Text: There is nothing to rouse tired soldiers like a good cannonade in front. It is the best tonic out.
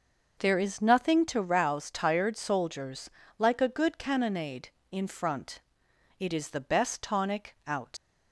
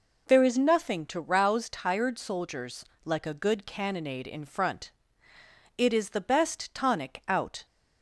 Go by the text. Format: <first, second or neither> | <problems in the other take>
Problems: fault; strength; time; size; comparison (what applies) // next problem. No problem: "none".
second | pauses between "soldiers" and "like"; slight; at 3.0 s; 0.30 s long; slight in the second // leaves "out" unfinished; at 7.9 s; 85 ms